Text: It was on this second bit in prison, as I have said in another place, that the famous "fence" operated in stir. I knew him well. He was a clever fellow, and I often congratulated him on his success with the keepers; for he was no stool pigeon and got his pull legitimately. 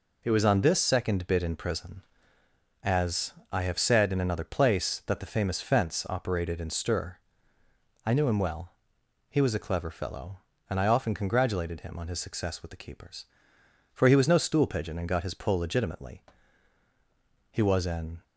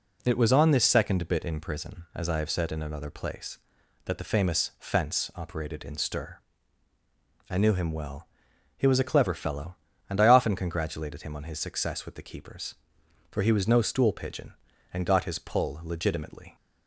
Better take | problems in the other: second | pauses between "as" and "I"; slight; at 3.3 s; 0.18 s long // goes on to say "He was an"; noticeable; from 17.5 s on; 0.72 s long

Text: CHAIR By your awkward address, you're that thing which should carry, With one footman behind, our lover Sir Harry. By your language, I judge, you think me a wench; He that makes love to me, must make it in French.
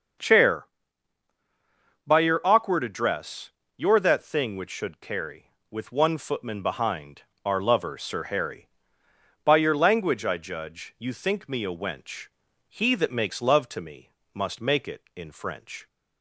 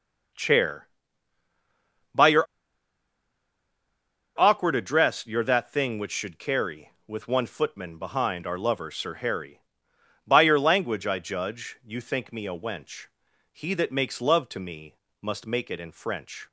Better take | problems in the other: first | starts louder than the rest; until 4.5 s; 6.5 dB; also in the first // pauses between "your" and "awkward"; strong; at 2.4 s; 1.9 s long

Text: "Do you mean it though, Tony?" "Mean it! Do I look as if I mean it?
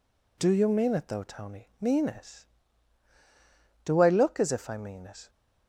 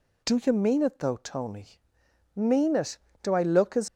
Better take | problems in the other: first | stops before "if I mean it"; at 3.8 s

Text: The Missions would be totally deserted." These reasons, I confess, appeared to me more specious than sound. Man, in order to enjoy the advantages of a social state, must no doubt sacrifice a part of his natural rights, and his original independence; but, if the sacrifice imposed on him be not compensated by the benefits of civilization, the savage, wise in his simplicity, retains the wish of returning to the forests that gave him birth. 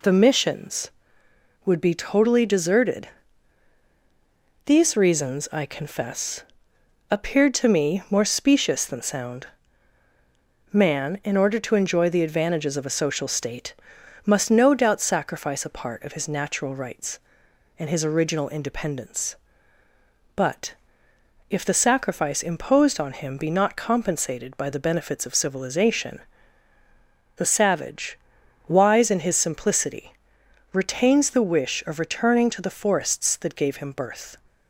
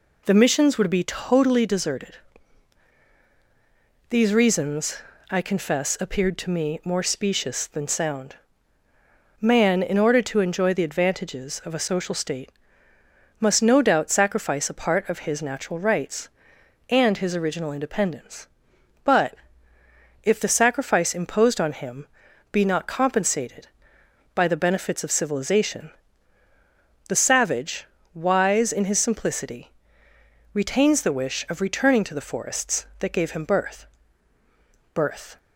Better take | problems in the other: first | pauses between "him" and "be"; noticeable; at 22.0 s; 0.46 s long // says "birth" twice; at 34.9 s

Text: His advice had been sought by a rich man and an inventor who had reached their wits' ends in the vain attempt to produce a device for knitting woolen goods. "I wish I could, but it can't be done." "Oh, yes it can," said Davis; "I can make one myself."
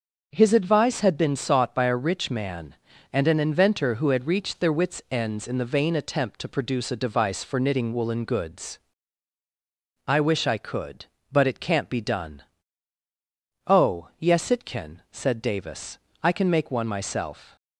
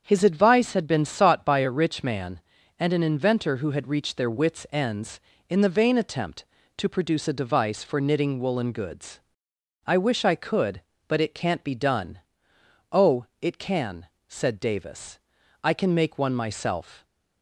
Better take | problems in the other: first | starts louder than the rest; strong; until 1.0 s; 7.5 dB; also in the first // skips "yes"; at 13.3 s

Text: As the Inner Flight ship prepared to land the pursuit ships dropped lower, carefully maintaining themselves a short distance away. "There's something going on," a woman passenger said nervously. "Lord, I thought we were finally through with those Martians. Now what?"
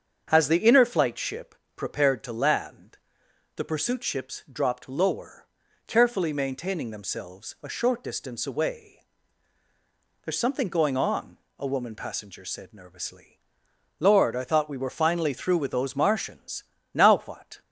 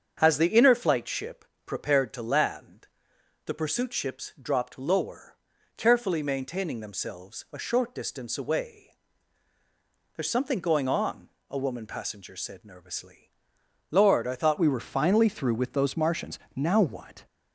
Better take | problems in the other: first | starts louder than the rest; strong; until 1.2 s; 7 dB; strong in the first // pauses between "ship" and "prepared"; slight; at 1.4 s; 0.20 s long; slight in the first // pauses between "land" and "the"; noticeable; at 2.8 s; 0.56 s long; noticeable in the first // changes voice at "we"; from 14.5 s on; 2.7 s long

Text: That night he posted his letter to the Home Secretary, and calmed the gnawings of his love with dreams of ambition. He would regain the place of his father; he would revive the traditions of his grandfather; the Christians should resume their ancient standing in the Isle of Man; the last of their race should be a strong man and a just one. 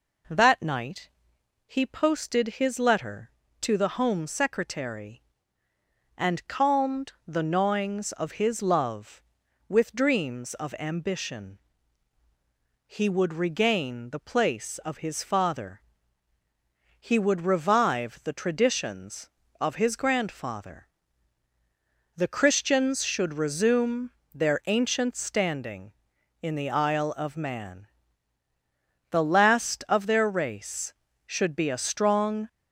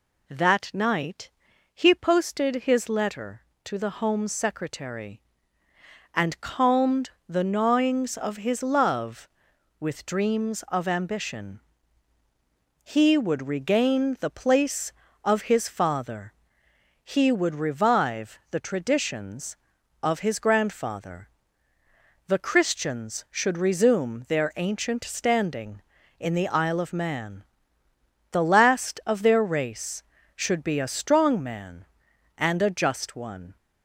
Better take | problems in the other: second | pauses between "night" and "he"; noticeable; at 1.0 s; 0.56 s long; also in the second // pauses between "calmed" and "the"; slight; at 7.1 s; 0.16 s long; slight in the second // pauses between "resume" and "their"; slight; at 24.0 s; 0.24 s long // stops before "man and a just one"; at 32.4 s

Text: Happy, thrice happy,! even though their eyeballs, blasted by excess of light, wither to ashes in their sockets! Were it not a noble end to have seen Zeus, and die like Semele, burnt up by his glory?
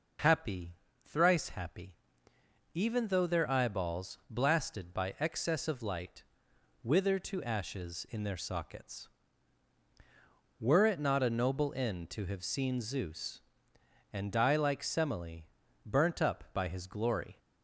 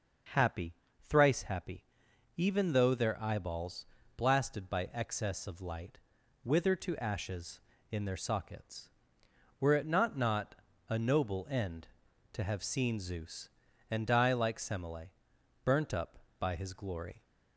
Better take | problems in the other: first | says "not" twice; at 10.1 s

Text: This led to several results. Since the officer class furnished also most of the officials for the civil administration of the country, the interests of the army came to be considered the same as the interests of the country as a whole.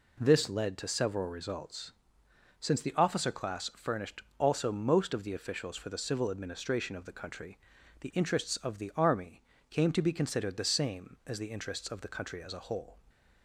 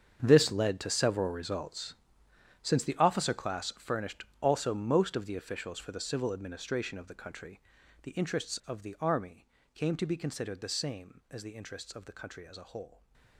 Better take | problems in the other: first | gets quieter; strong; throughout; 15 dB // pauses between "furnished" and "also"; slight; at 4.2 s; 0.16 s long; slight in the first // pauses between "army" and "came"; slight; at 9.4 s; 0.28 s long; slight in the first // stays silent after the last word; slight; from 12.8 s on; 0.5 s long

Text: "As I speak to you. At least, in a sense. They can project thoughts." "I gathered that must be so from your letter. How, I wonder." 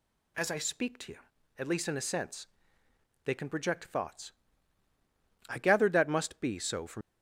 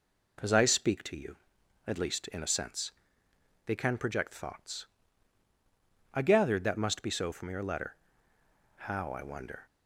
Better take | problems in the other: second | stops before "your letter How I wonder"; at 7.0 s

